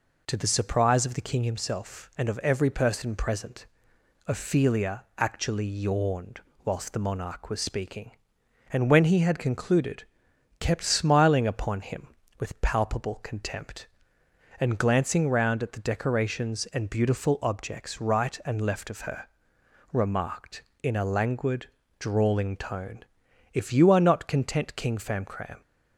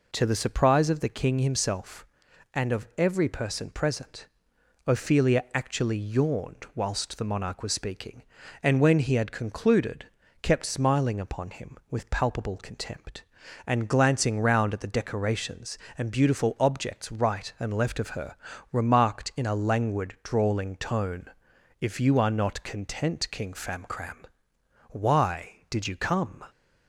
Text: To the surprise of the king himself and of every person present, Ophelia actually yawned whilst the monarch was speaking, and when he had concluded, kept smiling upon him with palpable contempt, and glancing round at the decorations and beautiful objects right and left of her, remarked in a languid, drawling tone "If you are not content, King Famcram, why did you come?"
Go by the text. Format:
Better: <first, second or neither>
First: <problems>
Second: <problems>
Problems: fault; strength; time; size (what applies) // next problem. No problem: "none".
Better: second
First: pauses between "yawned" and "whilst"; slight; at 6.3 s; 0.26 s long // pauses between "tone" and "If"; noticeable; at 23.0 s; 0.50 s long // stops before "why did you come"; at 25.6 s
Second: pauses between "tone" and "If"; noticeable; at 21.2 s; 0.54 s long